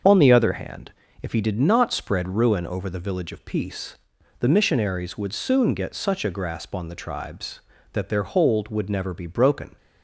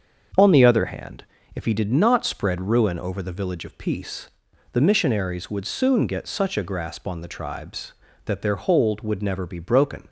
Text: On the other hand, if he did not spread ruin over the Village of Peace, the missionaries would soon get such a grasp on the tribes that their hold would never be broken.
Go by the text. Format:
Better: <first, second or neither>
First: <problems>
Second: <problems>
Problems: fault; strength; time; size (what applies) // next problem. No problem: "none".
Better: second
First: loses the start of "On"; at 0.0 s; 30 ms // starts louder than the rest; until 1.3 s; 7 dB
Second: starts louder than the rest; until 1.6 s; 7 dB